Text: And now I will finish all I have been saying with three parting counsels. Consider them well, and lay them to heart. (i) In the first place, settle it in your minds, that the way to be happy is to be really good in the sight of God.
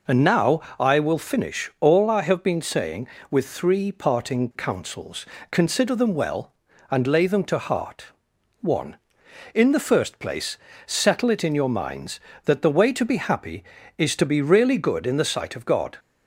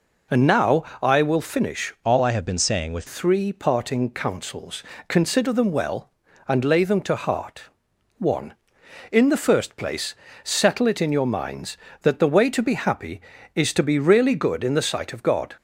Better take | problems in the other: first | pauses between "now" and "I"; slight; at 0.8 s; 0.20 s long; slight in the first // changes voice from "all" to "with"; from 2.0 to 3.0 s; 1.0 s long

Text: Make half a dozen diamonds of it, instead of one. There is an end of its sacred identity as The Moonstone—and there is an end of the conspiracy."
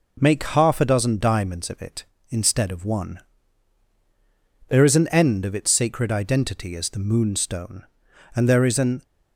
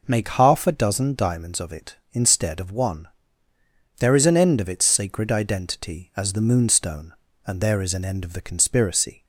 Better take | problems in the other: second | stops before "end of the conspiracy"; at 9.0 s

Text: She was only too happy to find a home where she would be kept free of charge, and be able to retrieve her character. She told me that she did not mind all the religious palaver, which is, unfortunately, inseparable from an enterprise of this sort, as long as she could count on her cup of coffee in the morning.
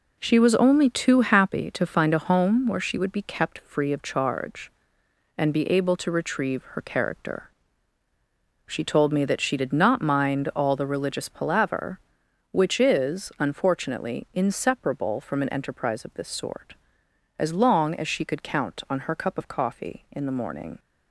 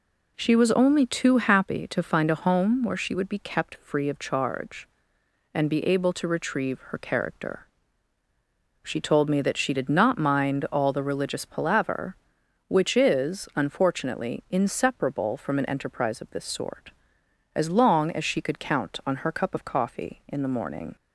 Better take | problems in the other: second | gets quieter; throughout; 7 dB

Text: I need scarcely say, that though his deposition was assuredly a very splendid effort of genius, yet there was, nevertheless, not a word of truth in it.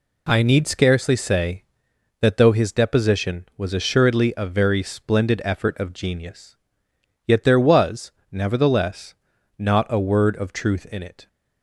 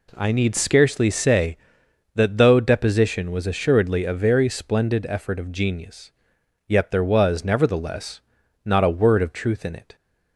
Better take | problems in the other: first | skips "his"; at 2.5 s

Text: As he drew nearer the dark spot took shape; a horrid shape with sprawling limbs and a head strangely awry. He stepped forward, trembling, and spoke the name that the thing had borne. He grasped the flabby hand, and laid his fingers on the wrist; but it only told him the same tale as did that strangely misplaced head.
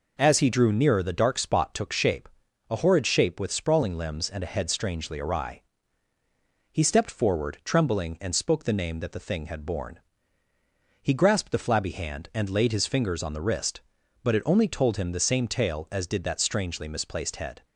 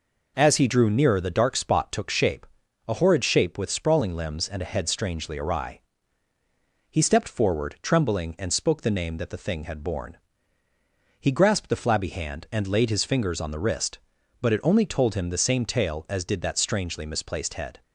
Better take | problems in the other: neither | none

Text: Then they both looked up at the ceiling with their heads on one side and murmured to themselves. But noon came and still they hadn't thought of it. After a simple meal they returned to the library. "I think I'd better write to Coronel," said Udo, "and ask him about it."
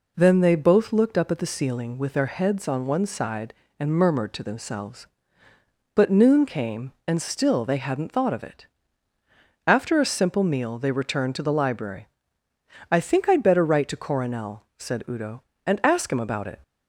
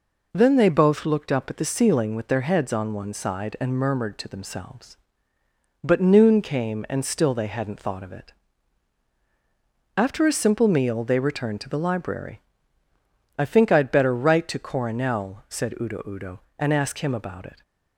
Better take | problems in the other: first | says "Udo" twice; at 16.0 s

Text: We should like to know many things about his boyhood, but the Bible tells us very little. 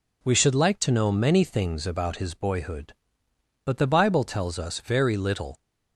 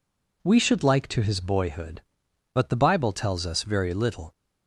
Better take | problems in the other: first | skips "know many things about"; at 1.2 s

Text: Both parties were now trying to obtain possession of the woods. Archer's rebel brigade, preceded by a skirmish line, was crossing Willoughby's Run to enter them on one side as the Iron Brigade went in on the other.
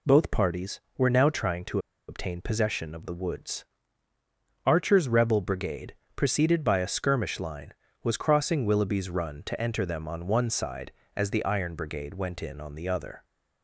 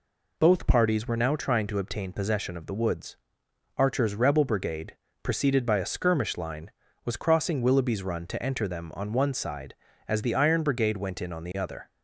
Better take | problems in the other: second | pauses between "to" and "obtain"; slight; at 1.7 s; 0.30 s long

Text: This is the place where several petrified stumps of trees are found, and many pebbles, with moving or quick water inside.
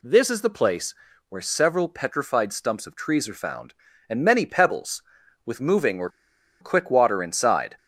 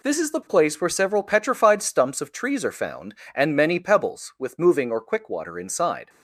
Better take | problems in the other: second | pauses between "place" and "where"; slight; at 0.9 s; 0.34 s long // pauses between "or" and "quick"; noticeable; at 6.0 s; 0.52 s long

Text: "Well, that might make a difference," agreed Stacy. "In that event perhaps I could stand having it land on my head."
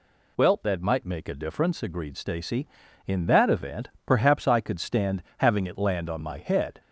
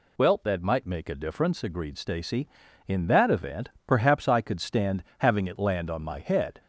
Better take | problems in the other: neither | pauses between "event" and "perhaps"; slight; the same in both

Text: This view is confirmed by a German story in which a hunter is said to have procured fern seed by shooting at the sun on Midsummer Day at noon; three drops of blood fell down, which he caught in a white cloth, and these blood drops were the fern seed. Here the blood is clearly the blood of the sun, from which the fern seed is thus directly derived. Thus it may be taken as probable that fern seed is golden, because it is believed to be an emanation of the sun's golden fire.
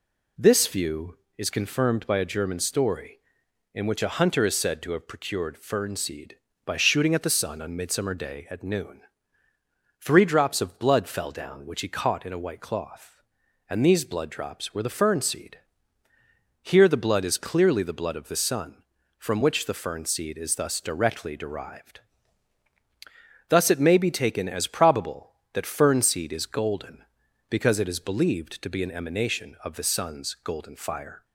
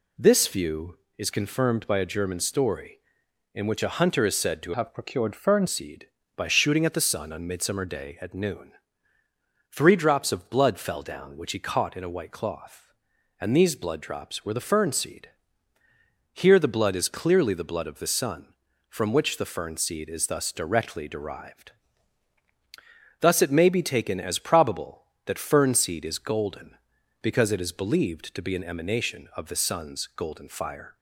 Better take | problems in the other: first | changes voice from "have" to "fern"; from 4.7 to 5.6 s; 0.9 s long

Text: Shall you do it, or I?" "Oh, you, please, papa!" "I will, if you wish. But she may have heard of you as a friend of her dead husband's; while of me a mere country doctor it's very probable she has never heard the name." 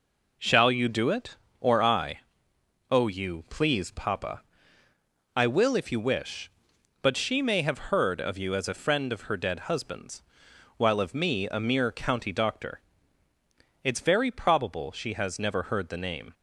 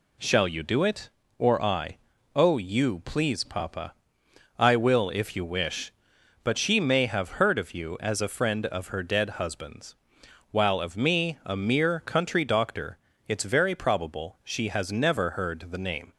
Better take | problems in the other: second | says "county" for "country"; at 11.9 s // pauses between "doctor" and "it's"; at 12.7 s; 1.0 s long; slight in the second

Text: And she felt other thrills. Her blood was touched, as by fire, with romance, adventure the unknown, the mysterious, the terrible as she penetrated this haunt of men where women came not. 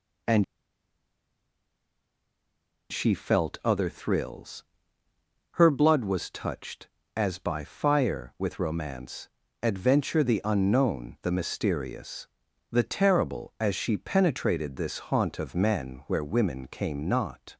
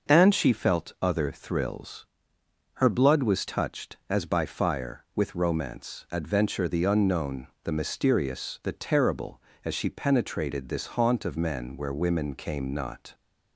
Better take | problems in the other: second | pauses between "And" and "she"; strong; at 0.4 s; 2.4 s long

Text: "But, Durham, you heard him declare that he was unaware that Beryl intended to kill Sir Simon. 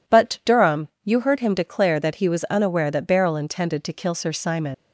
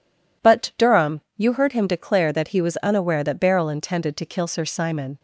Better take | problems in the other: second | leaves "Simon" unfinished; at 4.7 s; 120 ms

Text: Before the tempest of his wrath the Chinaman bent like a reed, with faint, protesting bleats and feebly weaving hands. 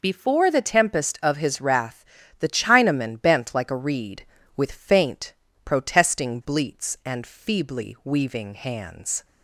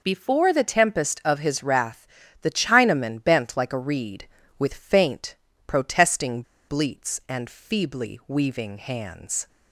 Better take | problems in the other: first | pauses between "wrath" and "the"; slight; at 2.0 s; 0.36 s long; slight in the first // pauses between "protesting" and "bleats"; slight; at 6.4 s; 0.25 s long

